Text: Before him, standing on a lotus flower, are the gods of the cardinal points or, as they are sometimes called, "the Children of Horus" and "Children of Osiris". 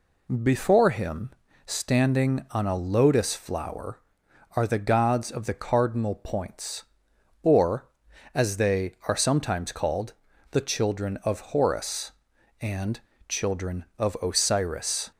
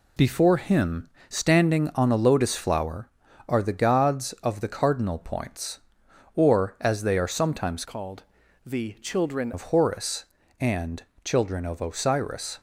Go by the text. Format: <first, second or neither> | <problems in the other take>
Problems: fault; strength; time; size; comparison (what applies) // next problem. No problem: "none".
first | changes voice from "called" to "Children"; from 7.8 to 9.5 s; 1.7 s long // pauses between "and" and "Children"; slight; at 11.0 s; 0.20 s long; slight in the first